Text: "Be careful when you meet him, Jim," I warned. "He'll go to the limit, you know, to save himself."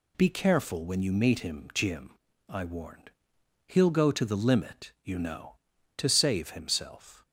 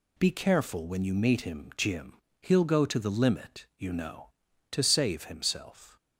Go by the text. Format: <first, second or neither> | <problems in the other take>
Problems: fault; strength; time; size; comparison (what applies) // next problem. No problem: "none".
first | skips "I warned"; at 2.2 s